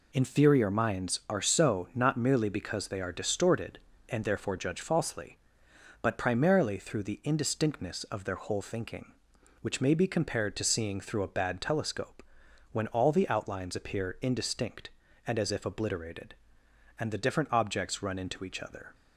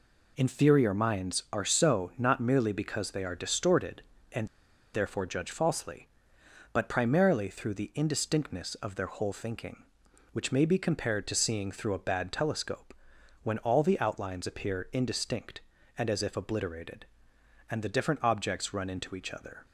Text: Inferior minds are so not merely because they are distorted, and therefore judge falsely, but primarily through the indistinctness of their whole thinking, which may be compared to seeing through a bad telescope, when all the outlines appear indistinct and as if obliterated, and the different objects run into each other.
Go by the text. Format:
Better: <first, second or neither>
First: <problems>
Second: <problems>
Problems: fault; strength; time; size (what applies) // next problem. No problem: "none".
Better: first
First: none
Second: pauses between "and" and "therefore"; noticeable; at 4.4 s; 0.46 s long